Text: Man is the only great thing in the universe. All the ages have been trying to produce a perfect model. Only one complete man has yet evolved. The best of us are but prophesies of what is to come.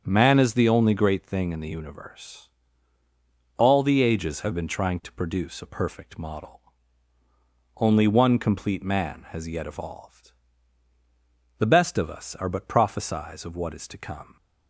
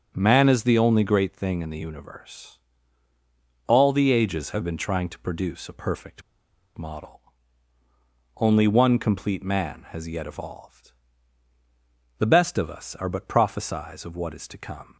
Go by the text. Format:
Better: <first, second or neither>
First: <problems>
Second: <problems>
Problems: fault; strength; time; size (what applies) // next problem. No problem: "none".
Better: first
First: starts louder than the rest; strong; until 1.0 s; 7.5 dB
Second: starts louder than the rest; strong; until 1.1 s; 7.5 dB // pauses between "perfect" and "model"; noticeable; at 6.2 s; 0.56 s long